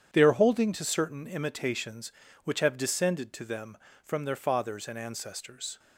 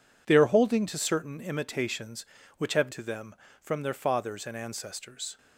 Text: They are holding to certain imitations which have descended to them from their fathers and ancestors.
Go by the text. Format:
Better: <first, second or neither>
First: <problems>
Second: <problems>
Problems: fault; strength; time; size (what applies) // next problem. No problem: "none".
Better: first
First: none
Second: skips "descended"; at 2.9 s